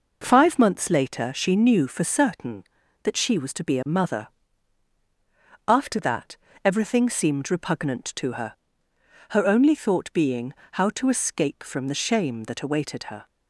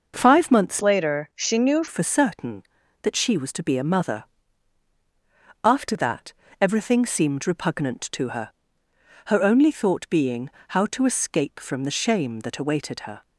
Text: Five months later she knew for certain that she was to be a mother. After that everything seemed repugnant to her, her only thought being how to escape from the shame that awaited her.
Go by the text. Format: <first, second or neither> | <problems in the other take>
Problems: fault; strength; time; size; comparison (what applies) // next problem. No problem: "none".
first | changes voice from "later" to "knew"; from 0.8 to 1.8 s; 1.0 s long // pauses between "that" and "everything"; slight; at 6.3 s; 0.28 s long; slight in the first // pauses between "being" and "how"; slight; at 10.4 s; 0.20 s long; slight in the first